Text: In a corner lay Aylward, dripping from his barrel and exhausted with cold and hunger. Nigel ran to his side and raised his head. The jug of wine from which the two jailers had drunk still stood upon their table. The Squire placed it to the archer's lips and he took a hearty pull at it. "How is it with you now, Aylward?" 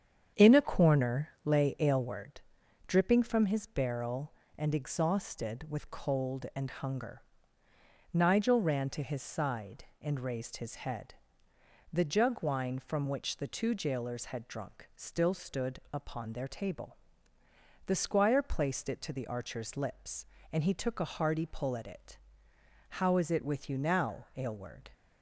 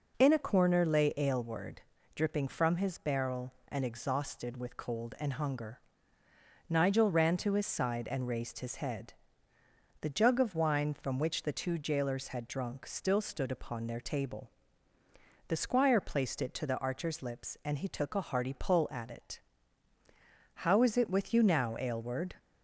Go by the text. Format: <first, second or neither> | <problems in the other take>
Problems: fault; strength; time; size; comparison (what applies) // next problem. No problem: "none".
second | starts louder than the rest; strong; until 1.5 s; 8 dB // pauses between "corner" and "lay"; slight; at 1.2 s; 0.16 s long // skips "of"; at 12.4 s